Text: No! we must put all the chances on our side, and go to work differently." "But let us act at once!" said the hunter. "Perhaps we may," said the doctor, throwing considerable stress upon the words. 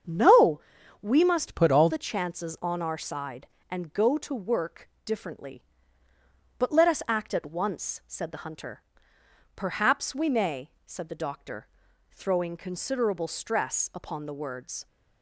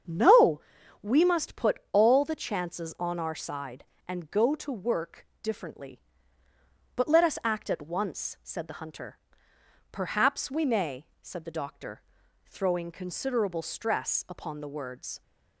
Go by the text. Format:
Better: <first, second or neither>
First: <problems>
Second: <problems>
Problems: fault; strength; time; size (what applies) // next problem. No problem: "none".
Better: second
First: starts louder than the rest; strong; until 1.4 s; 7.5 dB // changes voice from "put" to "all"; from 1.5 to 1.8 s; 0.3 s long // pauses between "work" and "differently"; slight; at 4.8 s; 0.16 s long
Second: starts louder than the rest; strong; until 1.4 s; 7.5 dB // pauses between "work" and "differently"; slight; at 5.2 s; 0.16 s long